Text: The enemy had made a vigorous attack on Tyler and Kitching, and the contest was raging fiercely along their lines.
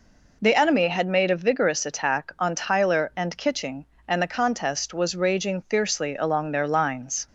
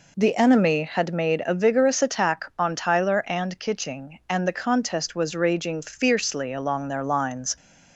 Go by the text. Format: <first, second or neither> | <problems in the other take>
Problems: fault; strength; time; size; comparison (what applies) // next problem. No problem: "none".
neither | none